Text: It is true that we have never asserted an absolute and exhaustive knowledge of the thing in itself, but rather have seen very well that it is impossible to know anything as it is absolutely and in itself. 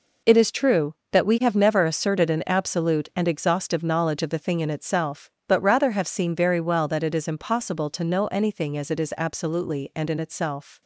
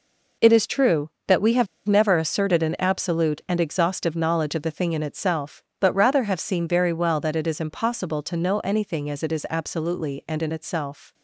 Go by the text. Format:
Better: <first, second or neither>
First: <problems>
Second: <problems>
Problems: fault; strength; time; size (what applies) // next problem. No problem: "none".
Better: first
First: none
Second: pauses between "have" and "never"; slight; at 1.6 s; 0.20 s long